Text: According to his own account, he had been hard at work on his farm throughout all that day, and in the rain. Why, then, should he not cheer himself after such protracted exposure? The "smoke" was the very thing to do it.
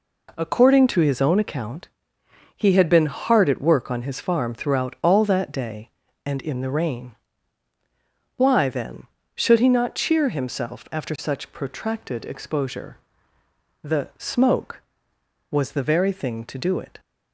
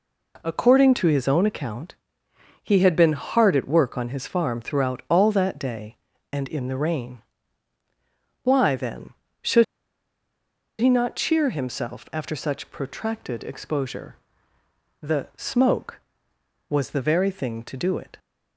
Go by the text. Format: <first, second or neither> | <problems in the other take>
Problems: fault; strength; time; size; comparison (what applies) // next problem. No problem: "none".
first | pauses between "should" and "he"; at 9.6 s; 1.1 s long